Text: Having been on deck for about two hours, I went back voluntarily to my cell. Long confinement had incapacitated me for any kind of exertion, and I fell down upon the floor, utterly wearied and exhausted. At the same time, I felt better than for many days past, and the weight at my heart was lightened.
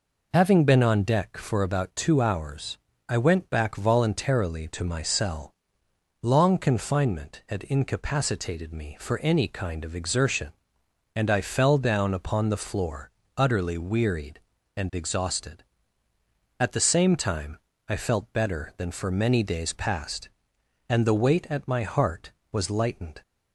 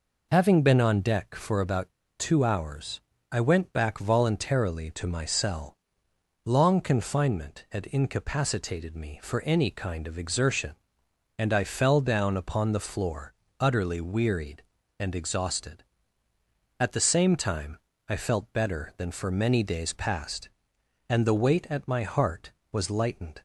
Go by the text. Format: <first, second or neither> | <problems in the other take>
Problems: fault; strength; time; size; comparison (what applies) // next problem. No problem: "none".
first | pauses between "about" and "two"; slight; at 1.9 s; 0.26 s long